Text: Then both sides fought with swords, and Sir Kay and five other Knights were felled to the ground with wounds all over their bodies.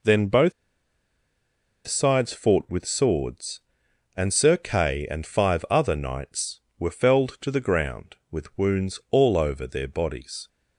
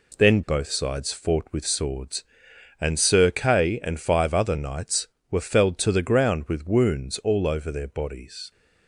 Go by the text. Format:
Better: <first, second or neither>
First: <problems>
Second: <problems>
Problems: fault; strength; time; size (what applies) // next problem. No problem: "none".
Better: second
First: pauses between "both" and "sides"; strong; at 0.5 s; 1.3 s long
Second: none